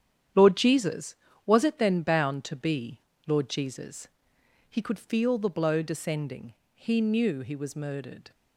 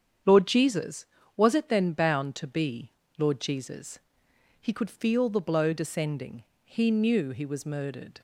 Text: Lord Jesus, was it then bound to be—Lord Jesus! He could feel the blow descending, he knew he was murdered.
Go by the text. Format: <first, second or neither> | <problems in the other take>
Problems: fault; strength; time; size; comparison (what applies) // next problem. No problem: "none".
second | gets quieter; strong; throughout; 9 dB // starts louder than the rest; strong; until 1.6 s; 9.5 dB; strong in the second